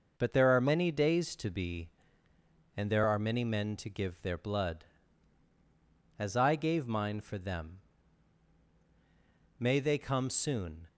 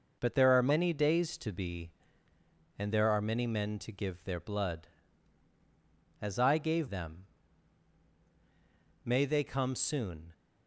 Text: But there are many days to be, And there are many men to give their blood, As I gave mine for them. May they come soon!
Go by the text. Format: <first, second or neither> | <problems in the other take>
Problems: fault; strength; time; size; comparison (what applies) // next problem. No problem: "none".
first | skips "mine for"; at 6.8 s